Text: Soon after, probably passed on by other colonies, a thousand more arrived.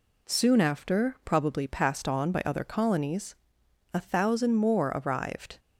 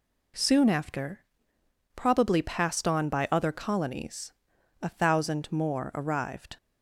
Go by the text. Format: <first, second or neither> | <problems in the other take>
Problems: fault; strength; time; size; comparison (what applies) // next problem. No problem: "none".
neither | none